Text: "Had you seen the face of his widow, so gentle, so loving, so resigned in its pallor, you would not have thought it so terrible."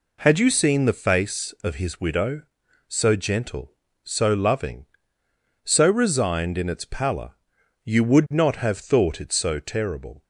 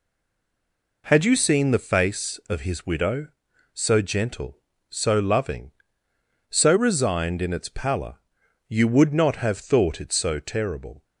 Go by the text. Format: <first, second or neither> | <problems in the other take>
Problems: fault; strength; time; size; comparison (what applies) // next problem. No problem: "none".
first | stays silent before the first word; until 1.0 s; 1.0 s long